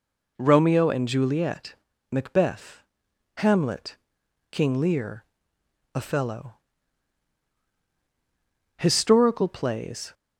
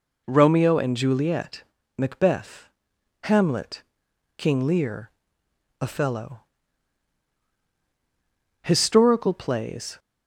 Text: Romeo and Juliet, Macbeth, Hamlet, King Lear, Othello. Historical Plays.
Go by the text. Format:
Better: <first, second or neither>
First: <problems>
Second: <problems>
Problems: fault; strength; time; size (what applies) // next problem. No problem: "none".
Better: neither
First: none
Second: none